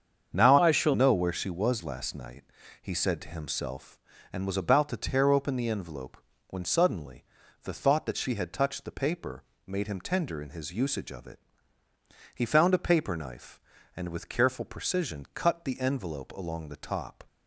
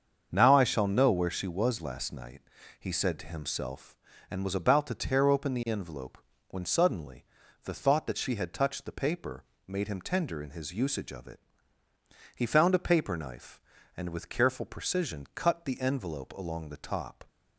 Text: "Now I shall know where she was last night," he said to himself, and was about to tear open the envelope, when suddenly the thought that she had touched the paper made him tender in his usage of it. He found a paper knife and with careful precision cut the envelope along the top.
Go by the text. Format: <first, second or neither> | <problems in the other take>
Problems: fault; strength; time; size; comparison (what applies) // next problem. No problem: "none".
second | starts louder than the rest; strong; until 1.3 s; 7.5 dB; also in the second // changes voice from "I" to "shall"; from 0.5 to 0.9 s; 0.4 s long // pauses between "suddenly" and "the"; at 7.2 s; 0.40 s long; also in the second // pauses between "paper" and "made"; slight; at 9.4 s; 0.24 s long; slight in the second